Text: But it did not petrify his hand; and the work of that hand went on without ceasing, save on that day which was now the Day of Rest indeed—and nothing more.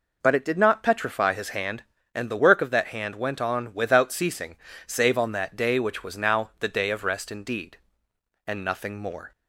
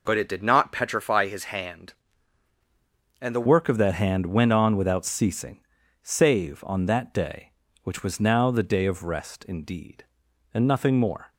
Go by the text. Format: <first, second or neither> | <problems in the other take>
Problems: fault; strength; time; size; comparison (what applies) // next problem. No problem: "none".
first | changes voice at "work"; from 3.4 s on; 7.9 s long